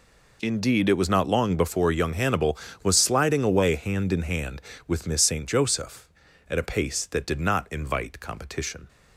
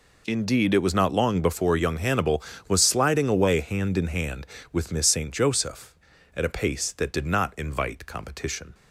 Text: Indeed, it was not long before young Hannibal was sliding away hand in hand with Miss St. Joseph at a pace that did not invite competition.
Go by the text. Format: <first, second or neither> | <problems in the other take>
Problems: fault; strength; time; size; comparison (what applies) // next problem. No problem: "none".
neither | none